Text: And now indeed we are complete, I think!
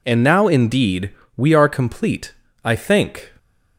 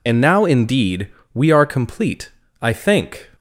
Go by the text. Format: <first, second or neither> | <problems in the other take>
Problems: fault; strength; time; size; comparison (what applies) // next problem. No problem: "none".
first | loses the start of "And"; at 0.0 s; 40 ms // pauses between "indeed" and "we"; slight; at 1.0 s; 0.26 s long; slight in the first